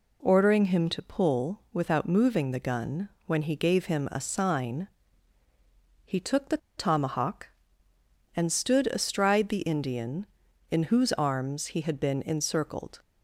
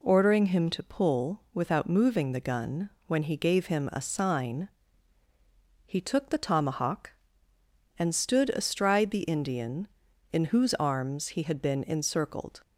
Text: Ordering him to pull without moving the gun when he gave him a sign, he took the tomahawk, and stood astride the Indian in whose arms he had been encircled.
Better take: second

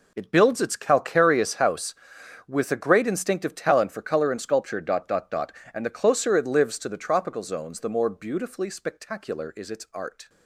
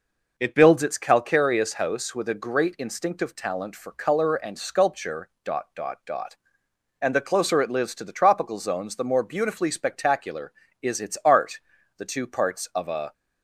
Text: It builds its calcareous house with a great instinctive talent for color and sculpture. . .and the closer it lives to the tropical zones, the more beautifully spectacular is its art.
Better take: first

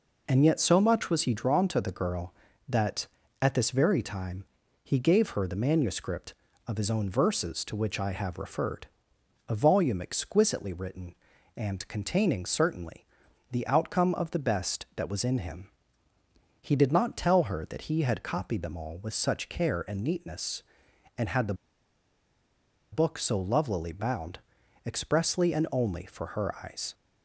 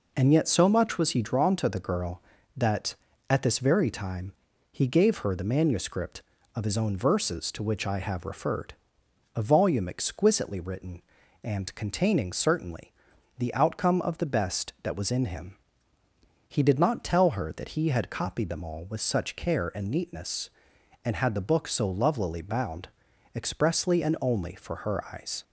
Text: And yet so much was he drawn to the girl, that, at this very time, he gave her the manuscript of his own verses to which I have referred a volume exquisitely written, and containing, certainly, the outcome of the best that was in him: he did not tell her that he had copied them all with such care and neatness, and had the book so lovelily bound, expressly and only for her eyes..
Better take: second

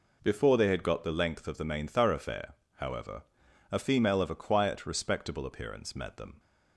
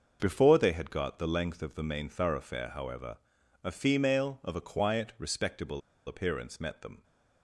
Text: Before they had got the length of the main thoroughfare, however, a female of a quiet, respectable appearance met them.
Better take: first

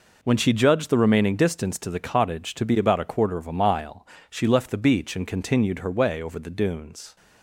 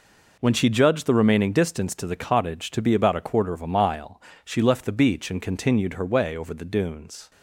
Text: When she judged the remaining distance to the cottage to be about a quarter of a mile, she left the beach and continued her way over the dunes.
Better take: neither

